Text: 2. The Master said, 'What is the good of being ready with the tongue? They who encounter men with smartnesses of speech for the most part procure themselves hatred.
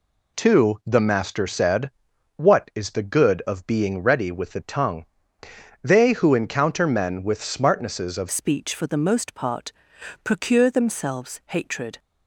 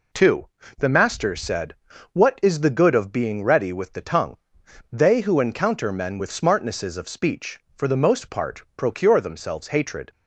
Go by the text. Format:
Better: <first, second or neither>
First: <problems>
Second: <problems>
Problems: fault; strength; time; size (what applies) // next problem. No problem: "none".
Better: second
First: changes voice at "speech"; from 8.3 s on; 3.6 s long // pauses between "part" and "procure"; noticeable; at 9.7 s; 0.52 s long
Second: none